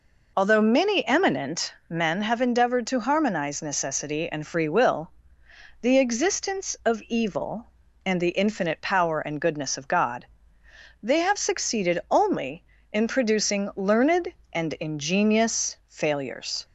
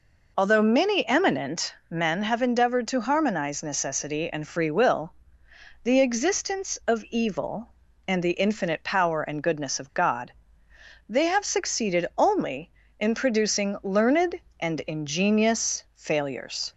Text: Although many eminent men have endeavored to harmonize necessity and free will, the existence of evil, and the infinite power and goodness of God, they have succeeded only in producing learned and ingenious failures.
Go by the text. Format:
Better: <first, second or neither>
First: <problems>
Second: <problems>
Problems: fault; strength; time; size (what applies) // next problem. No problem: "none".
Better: neither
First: pauses between "eminent" and "men"; slight; at 1.7 s; 0.16 s long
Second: pauses between "eminent" and "men"; slight; at 1.7 s; 0.16 s long